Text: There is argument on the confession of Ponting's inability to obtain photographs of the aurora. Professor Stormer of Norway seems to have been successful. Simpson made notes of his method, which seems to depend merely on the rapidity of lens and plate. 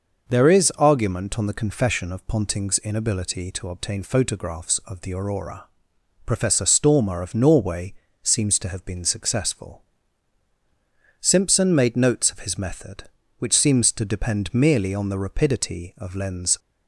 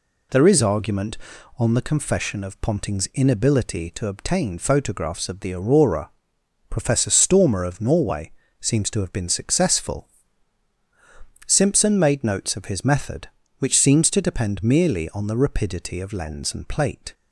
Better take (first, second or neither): second